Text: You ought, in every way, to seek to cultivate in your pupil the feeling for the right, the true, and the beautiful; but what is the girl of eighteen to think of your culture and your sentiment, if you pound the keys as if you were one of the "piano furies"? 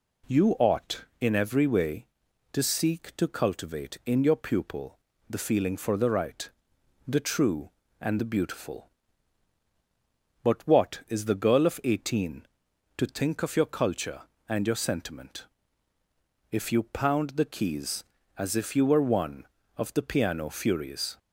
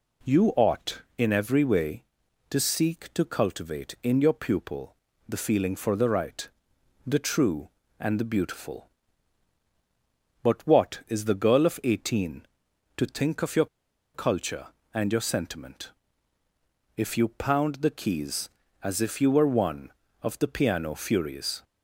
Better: first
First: pauses between "pupil" and "the"; slight; at 4.9 s; 0.32 s long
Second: pauses between "pupil" and "the"; slight; at 4.9 s; 0.34 s long // pauses between "your" and "culture"; noticeable; at 13.6 s; 0.48 s long

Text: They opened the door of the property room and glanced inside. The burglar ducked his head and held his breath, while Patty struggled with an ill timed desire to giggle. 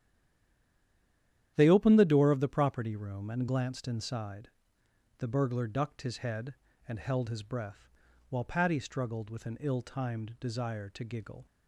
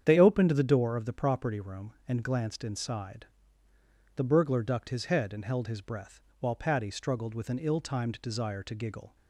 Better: second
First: stays silent before the first word; noticeable; until 1.5 s; 1.5 s long // starts louder than the rest; strong; until 2.5 s; 10.5 dB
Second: starts louder than the rest; strong; until 1.0 s; 8.5 dB

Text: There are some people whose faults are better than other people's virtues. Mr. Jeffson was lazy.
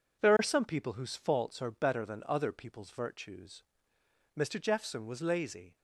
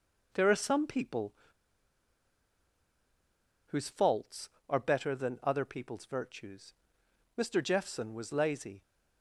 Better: first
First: none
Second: pauses between "people" and "whose"; strong; at 1.3 s; 2.3 s long

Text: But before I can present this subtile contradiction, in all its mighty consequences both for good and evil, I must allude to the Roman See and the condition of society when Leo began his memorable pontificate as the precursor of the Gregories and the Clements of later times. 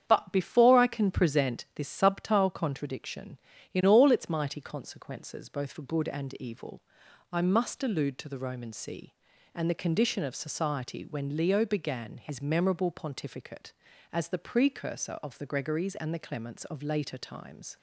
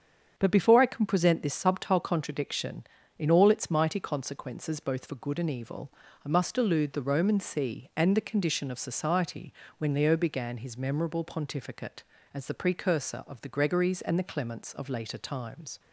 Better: first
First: starts louder than the rest; strong; until 1.0 s; 8.5 dB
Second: starts louder than the rest; strong; until 1.3 s; 7.5 dB // skips "to"; at 6.9 s // pauses between "society" and "when"; slight; at 9.5 s; 0.24 s long

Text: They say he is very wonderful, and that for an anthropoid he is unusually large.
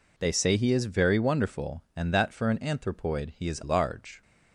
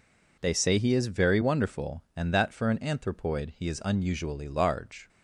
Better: second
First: skips "unusually"; at 3.6 s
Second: none

